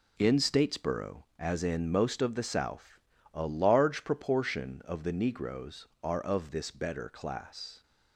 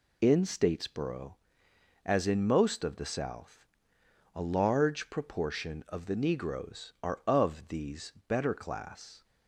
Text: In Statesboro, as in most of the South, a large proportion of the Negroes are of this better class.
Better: first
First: none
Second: says "these" for "this"; at 7.6 s

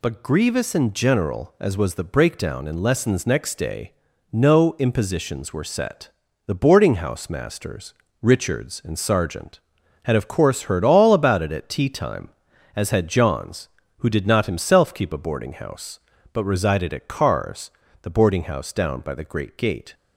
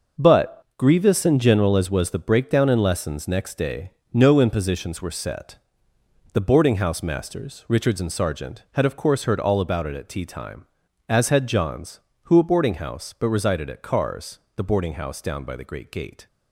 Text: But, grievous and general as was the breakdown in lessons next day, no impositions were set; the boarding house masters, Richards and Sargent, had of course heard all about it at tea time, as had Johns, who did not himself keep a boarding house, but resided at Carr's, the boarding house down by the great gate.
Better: first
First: none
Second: starts louder than the rest; noticeable; until 1.3 s; 6 dB // skips "did not himself keep"; at 12.3 s

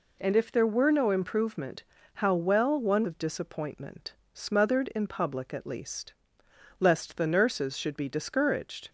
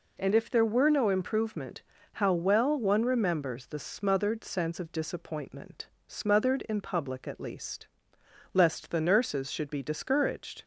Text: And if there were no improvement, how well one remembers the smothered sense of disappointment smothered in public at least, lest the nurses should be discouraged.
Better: second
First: skips "remembers the smothered sense"; at 3.0 s // pauses between "disappointment" and "smothered"; slight; at 4.1 s; 0.20 s long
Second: pauses between "disappointment" and "smothered"; slight; at 5.8 s; 0.20 s long

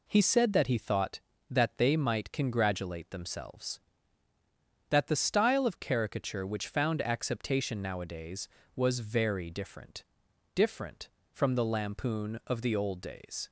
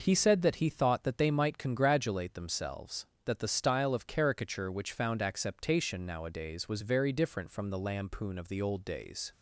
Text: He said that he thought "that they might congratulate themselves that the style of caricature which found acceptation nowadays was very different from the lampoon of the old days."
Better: second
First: says "different" twice; at 10.5 s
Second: none

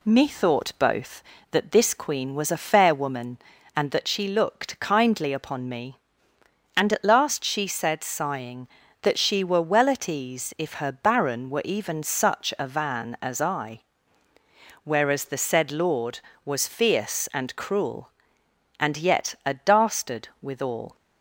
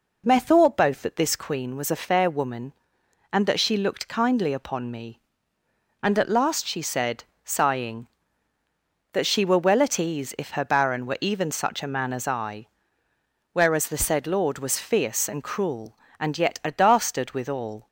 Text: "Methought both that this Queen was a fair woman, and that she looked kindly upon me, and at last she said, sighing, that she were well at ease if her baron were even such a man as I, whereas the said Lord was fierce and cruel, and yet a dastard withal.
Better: second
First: says "van" for "man"; at 12.6 s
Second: none

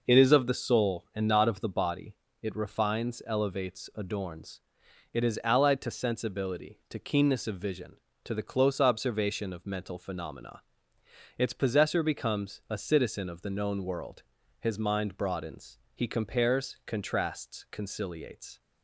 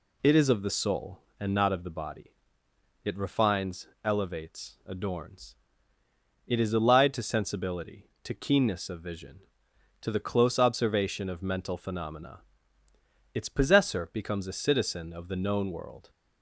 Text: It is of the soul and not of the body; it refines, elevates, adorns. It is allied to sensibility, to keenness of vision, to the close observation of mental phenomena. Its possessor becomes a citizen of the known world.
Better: second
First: goes on to say "His mind broadens he compares contrasts conciliates"; strong; from 14.6 s on; 4.0 s long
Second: none

